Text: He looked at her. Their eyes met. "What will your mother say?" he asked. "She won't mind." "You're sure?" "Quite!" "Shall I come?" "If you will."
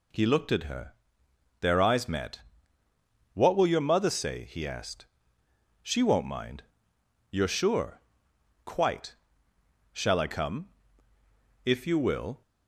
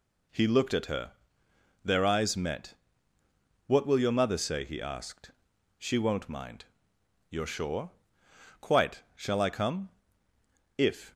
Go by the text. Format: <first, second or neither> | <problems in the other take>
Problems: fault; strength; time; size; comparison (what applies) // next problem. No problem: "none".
first | stops before "you will"; at 11.1 s